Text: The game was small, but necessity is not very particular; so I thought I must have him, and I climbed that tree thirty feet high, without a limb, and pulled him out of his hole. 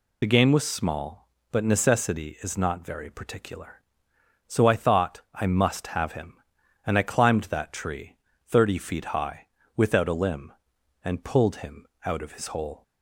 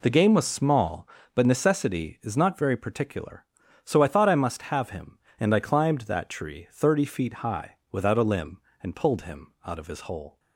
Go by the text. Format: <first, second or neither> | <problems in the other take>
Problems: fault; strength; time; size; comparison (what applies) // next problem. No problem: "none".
second | loses the start of "The"; at 0.2 s; 40 ms // pauses between "tree" and "thirty"; slight; at 8.1 s; 0.32 s long // pauses between "him" and "out"; slight; at 11.8 s; 0.20 s long